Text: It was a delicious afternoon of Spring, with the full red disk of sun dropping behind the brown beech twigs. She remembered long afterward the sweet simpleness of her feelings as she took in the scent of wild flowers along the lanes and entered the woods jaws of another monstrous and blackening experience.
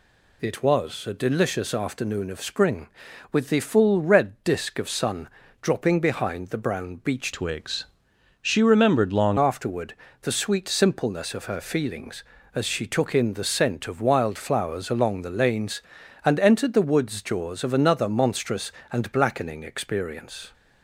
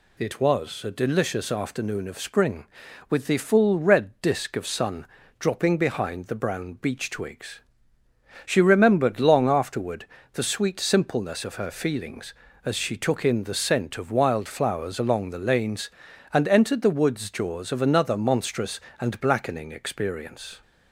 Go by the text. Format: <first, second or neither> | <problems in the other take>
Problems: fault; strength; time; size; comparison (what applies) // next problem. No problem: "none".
second | pauses between "sun" and "dropping"; slight; at 5.2 s; 0.32 s long; slight in the second // changes voice from "twigs" to "long"; from 7.3 to 9.3 s; 2.0 s long // pauses between "afterward" and "the"; slight; at 9.9 s; 0.26 s long; slight in the second